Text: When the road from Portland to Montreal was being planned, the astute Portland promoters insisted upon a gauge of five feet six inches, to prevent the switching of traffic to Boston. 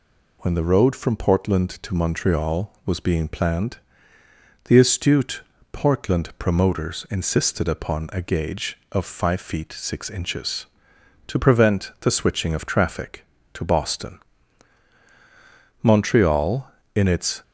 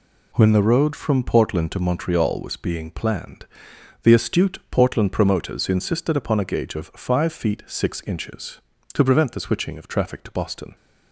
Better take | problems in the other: second | pauses between "astute" and "Portland"; slight; at 5.4 s; 0.32 s long // goes on to say "Montreal in its"; from 15.8 s on; 1.6 s long

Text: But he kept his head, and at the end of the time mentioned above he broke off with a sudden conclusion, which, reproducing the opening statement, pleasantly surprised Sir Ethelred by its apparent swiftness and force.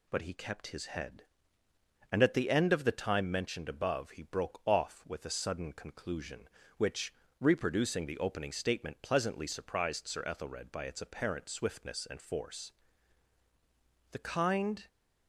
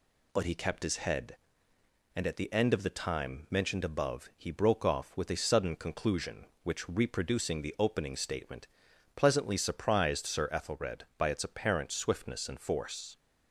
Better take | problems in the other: second | goes on to say "The kind"; noticeable; from 14.1 s on; 0.76 s long

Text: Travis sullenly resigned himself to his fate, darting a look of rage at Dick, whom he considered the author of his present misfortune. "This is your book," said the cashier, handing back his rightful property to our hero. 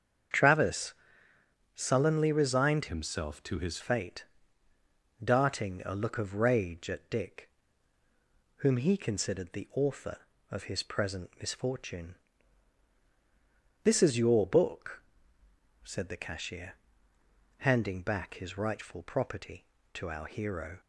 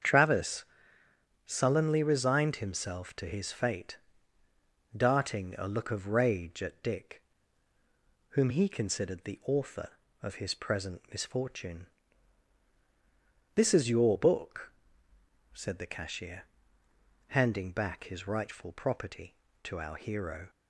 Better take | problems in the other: second | starts louder than the rest; strong; until 2.1 s; 7.5 dB; strong in the second // pauses between "Travis" and "sullenly"; noticeable; at 0.9 s; 0.80 s long; noticeable in the second // changes voice from "himself" to "his"; from 2.8 to 3.7 s; 0.9 s long

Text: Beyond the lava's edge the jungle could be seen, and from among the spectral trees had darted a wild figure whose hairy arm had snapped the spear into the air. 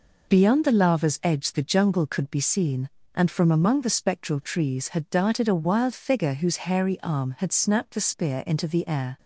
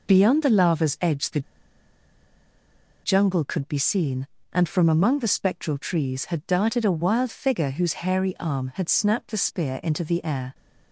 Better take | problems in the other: first | pauses between "the" and "jungle"; strong; at 1.4 s; 1.6 s long

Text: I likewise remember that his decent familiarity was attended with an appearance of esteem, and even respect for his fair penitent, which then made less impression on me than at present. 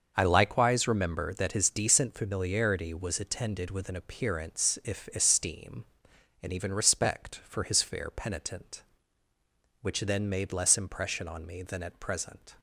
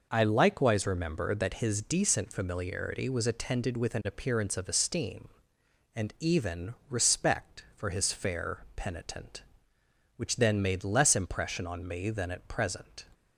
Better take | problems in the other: second | starts louder than the rest; until 1.1 s; 6.5 dB // says "if" for "of"; at 4.8 s

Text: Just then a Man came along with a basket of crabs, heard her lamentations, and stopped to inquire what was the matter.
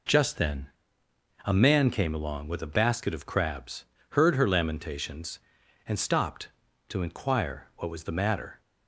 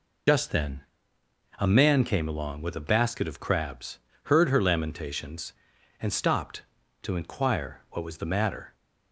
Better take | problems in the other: first | loses the start of "Just"; at 0.2 s; 70 ms // pauses between "then" and "a"; noticeable; at 0.8 s; 0.76 s long; noticeable in the first

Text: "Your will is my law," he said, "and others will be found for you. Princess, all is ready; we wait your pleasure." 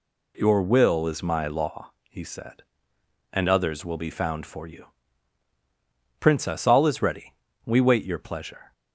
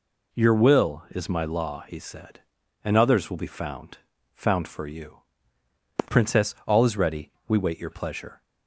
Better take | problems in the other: first | says "found" twice; at 4.3 s

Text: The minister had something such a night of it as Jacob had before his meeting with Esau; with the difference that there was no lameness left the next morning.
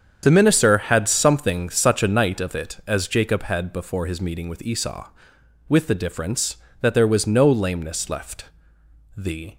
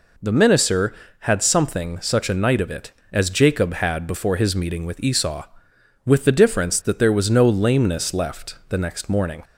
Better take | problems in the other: second | starts louder than the rest; strong; until 1.2 s; 7.5 dB // pauses between "left" and "the"; noticeable; at 8.4 s; 0.72 s long // stops before "next morning"; at 9.5 s

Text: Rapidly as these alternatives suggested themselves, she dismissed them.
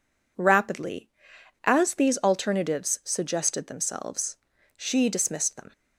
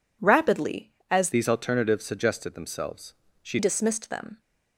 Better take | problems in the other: first | changes voice from "these" to "she"; from 1.3 to 3.5 s; 2.2 s long

